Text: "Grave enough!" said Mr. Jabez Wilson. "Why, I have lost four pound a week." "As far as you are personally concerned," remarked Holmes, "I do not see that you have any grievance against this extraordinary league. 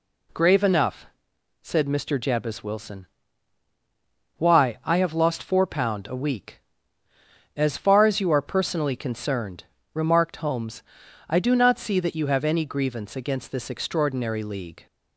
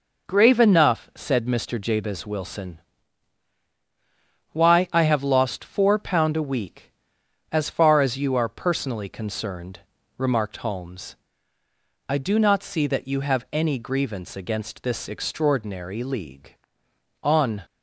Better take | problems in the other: first | goes on to say "On"; slight; from 17.2 s on; 0.40 s long

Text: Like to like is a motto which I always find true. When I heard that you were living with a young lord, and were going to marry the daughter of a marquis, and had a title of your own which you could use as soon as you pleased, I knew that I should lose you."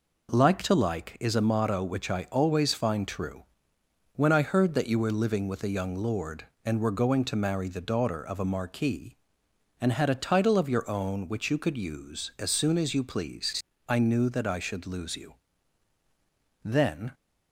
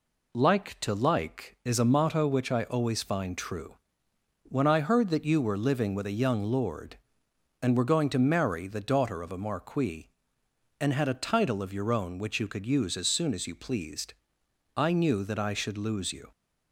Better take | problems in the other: second | goes on to say "Then"; from 16.6 s on; 0.50 s long

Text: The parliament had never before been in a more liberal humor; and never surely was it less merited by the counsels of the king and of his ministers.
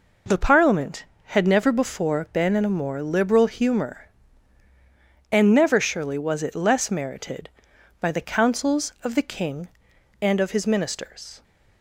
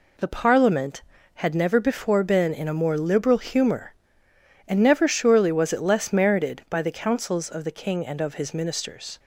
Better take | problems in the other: neither | none

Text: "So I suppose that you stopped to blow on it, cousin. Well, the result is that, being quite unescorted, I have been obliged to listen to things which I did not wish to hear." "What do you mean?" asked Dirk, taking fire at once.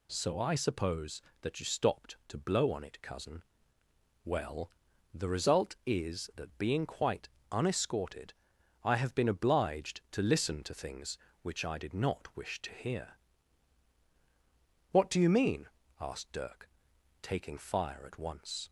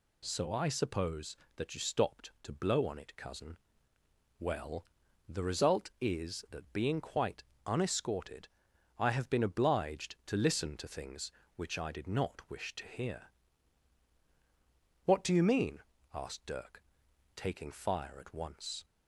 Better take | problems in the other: neither | pauses between "quite" and "unescorted"; slight; the same in both

